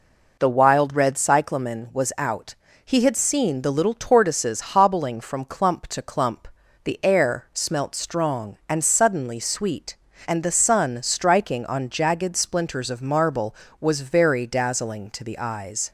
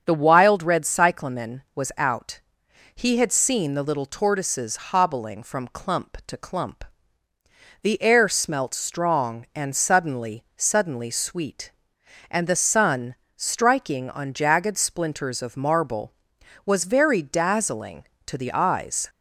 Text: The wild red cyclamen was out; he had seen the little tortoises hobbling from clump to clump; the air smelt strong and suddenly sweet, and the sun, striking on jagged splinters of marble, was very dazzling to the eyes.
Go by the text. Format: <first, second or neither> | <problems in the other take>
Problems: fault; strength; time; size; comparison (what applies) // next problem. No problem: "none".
first | starts louder than the rest; until 1.0 s; 7 dB // says "suddenly" twice; at 10.5 s